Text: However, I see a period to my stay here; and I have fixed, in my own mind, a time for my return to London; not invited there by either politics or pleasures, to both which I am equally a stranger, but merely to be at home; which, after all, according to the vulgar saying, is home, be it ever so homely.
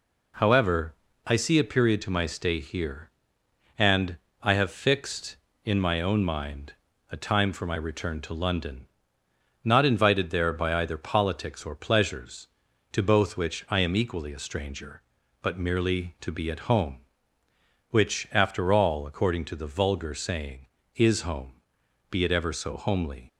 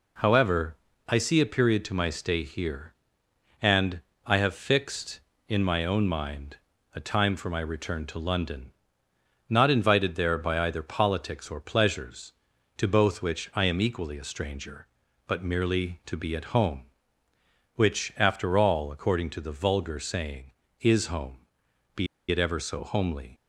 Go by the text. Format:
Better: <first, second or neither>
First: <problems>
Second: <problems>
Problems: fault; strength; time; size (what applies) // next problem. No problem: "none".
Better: first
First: pauses between "and" and "I"; slight; at 4.1 s; 0.24 s long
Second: pauses between "and" and "I"; slight; at 4.0 s; 0.24 s long // pauses between "be" and "it"; slight; at 22.0 s; 0.24 s long